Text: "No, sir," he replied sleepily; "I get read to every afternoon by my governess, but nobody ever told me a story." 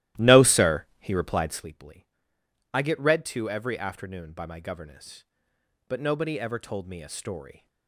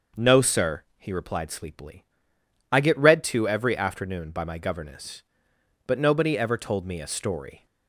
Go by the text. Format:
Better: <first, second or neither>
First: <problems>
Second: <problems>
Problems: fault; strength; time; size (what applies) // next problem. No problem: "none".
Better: second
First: starts louder than the rest; strong; until 1.8 s; 15 dB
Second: none